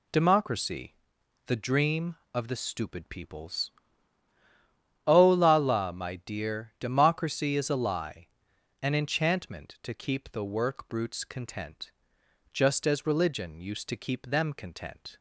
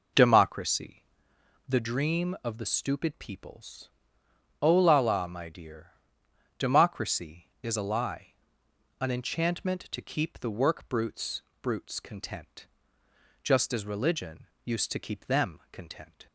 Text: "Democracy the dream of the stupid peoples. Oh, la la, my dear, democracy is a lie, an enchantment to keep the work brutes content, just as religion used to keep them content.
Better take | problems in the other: first | pauses between "Democracy" and "the"; noticeable; at 1.0 s; 0.64 s long; noticeable in the first // says "brutes" twice; at 11.6 s // pauses between "religion" and "used"; slight; at 14.4 s; 0.16 s long

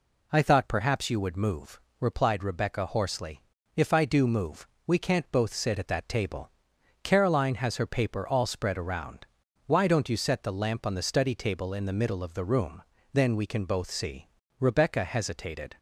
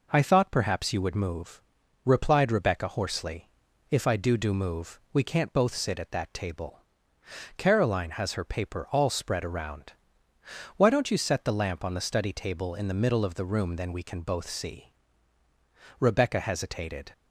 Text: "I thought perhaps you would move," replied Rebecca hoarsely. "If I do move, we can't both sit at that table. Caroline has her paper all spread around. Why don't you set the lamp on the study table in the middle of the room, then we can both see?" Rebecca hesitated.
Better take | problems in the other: first | says "do" twice; at 4.3 s

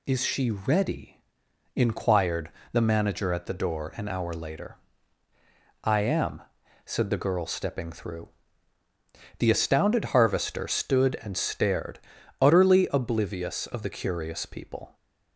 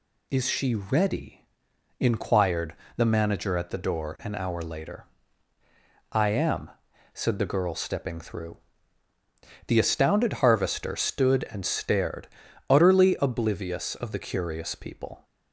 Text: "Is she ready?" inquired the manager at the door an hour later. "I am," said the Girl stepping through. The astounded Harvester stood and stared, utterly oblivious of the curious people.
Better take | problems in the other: neither | pauses between "inquired" and "the"; slight; the same in both

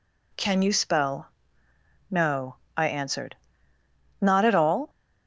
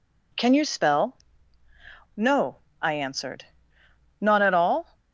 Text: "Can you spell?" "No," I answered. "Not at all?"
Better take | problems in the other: neither | none

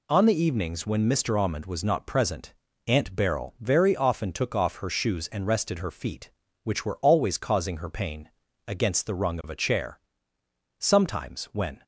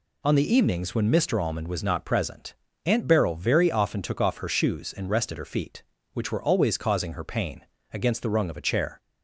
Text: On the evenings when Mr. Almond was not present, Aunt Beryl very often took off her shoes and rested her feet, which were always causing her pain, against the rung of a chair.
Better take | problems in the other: second | goes on to say "Sometimes when"; noticeable; from 10.7 s on; 1.0 s long

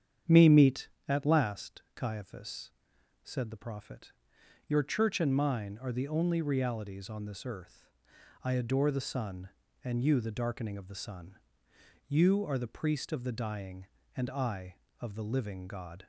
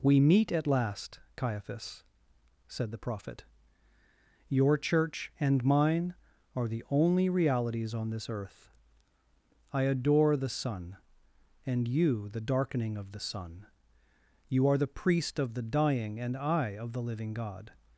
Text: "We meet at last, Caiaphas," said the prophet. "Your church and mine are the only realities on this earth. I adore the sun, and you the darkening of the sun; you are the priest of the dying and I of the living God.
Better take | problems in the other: second | starts louder than the rest; strong; until 1.4 s; 8.5 dB // says "Me" for "We"; at 0.2 s

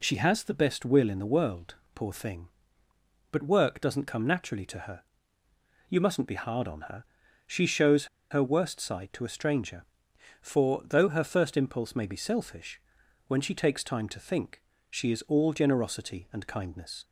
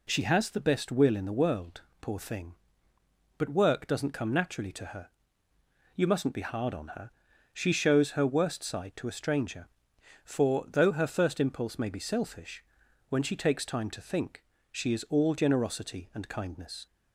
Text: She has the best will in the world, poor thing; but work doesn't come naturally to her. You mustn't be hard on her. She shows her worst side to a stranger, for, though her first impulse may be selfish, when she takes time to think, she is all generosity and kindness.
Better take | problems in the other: second | pauses between "shows" and "her"; slight; at 8.0 s; 0.25 s long

